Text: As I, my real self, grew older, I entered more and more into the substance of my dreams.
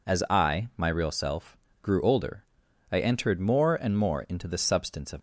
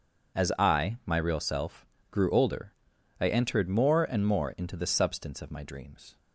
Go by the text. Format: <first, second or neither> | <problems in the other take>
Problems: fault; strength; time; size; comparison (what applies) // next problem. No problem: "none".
second | stops before "my dreams"; at 5.1 s